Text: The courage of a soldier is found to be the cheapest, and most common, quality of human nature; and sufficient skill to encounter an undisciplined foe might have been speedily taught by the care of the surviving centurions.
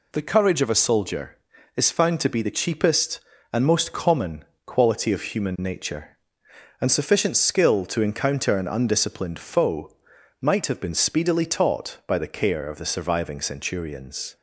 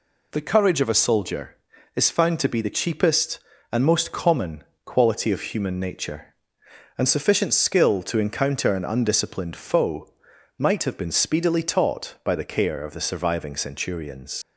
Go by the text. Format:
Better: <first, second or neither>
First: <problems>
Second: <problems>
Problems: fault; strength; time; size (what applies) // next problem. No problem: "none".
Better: first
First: pauses between "foe" and "might"; noticeable; at 9.8 s; 0.50 s long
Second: pauses between "foe" and "might"; noticeable; at 10.0 s; 0.50 s long // leaves "centurions" unfinished; at 14.4 s; 90 ms